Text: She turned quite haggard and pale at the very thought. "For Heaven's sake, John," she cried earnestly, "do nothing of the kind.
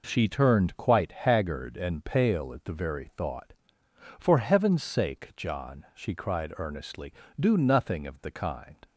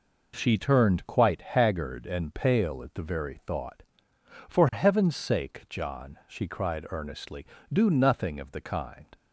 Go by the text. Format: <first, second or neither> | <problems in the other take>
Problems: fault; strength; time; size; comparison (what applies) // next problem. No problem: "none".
neither | none